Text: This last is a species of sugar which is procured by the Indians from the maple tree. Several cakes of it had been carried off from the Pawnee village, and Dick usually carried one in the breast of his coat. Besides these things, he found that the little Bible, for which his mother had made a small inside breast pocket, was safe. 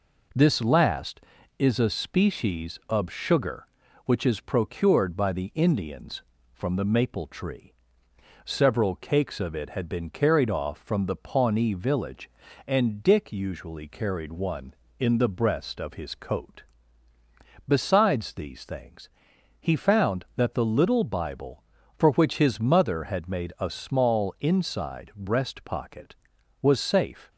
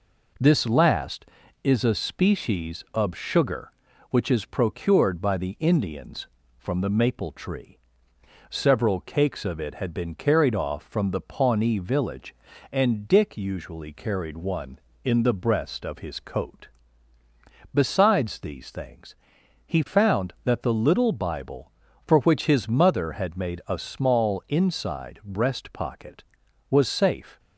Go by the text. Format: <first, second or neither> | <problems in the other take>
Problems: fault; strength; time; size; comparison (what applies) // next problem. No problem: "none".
neither | none